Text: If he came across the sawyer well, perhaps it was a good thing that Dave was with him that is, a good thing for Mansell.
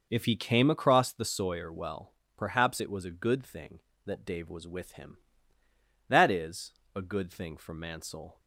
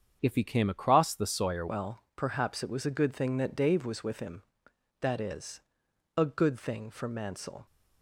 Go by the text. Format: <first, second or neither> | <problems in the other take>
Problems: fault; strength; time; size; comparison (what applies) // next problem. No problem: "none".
first | starts louder than the rest; strong; until 1.2 s; 7.5 dB // changes voice at "well"; from 1.6 s on; 6.0 s long